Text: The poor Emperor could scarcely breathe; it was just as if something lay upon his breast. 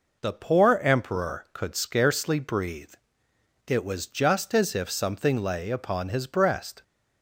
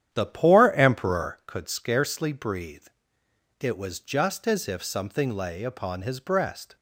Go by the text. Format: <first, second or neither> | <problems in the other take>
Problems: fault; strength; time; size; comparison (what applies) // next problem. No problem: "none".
first | starts louder than the rest; strong; until 1.5 s; 10 dB